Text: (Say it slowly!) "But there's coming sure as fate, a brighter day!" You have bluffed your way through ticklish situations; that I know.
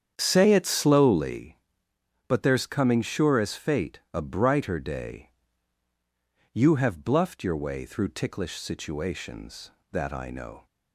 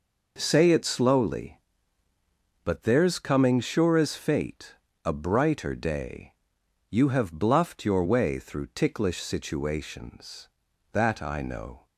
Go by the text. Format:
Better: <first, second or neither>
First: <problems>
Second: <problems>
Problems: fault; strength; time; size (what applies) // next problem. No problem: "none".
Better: second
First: starts louder than the rest; strong; until 1.4 s; 8.5 dB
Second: none